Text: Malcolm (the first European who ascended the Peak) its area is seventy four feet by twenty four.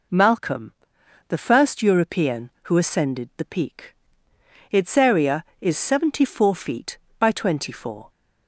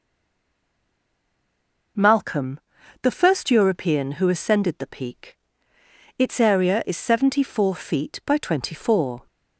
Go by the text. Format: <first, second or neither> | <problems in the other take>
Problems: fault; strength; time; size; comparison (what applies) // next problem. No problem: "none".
first | stays silent before the first word; noticeable; until 1.9 s; 1.9 s long